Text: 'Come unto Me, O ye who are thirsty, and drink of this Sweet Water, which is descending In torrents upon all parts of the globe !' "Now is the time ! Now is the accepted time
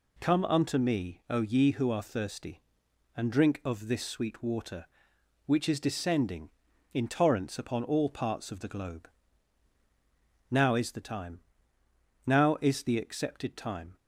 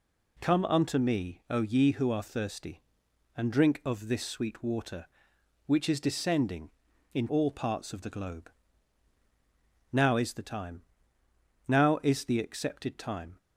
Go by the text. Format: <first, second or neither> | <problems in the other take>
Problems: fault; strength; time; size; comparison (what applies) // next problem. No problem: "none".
first | skips "torrents upon"; at 7.2 s